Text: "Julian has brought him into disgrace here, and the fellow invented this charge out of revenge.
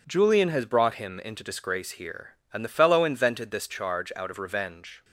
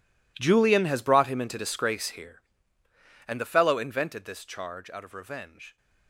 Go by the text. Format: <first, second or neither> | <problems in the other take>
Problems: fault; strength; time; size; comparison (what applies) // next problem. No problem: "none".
first | gets quieter; strong; throughout; 18.5 dB